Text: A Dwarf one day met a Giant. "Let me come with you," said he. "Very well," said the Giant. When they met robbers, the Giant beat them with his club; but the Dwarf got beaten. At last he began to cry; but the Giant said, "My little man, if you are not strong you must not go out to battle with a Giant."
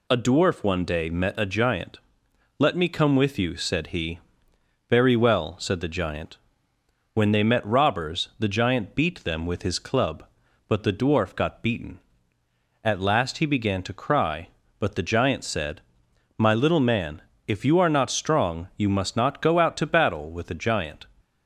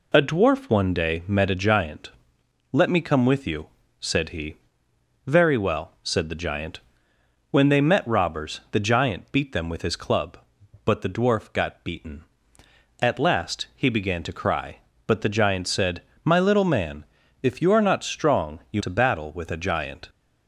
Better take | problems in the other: first | skips "must not go out"; at 18.8 s

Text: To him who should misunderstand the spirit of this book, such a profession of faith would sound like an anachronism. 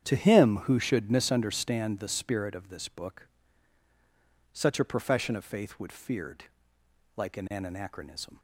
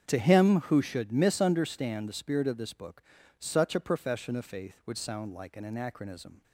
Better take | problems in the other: second | starts louder than the rest; strong; until 1.1 s; 9 dB; strong in the second // says "feared" for "sound"; at 5.9 s

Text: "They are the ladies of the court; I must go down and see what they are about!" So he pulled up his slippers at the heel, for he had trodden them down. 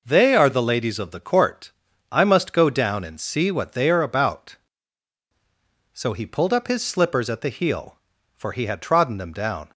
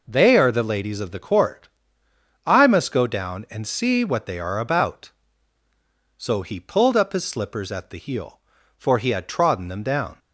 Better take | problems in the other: neither | none

